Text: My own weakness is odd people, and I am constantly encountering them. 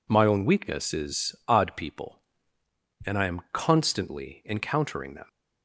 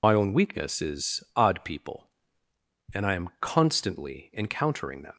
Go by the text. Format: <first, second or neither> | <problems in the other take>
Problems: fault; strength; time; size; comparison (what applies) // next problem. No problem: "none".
first | loses the start of "My"; at 0.0 s; 60 ms